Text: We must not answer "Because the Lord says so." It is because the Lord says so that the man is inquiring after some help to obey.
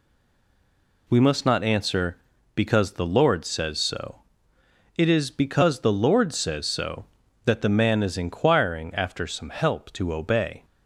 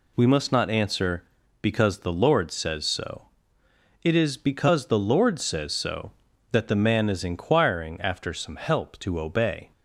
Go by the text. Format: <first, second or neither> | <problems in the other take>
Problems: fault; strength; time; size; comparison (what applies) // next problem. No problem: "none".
second | stays silent before the first word; until 1.0 s; 1.0 s long